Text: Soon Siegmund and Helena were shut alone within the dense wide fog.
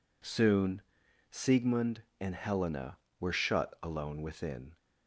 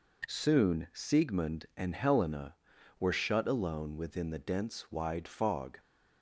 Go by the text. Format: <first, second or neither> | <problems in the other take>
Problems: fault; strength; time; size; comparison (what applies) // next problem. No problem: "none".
second | pauses between "Soon" and "Siegmund"; noticeable; at 0.8 s; 0.50 s long // stops before "the dense wide fog"; at 4.7 s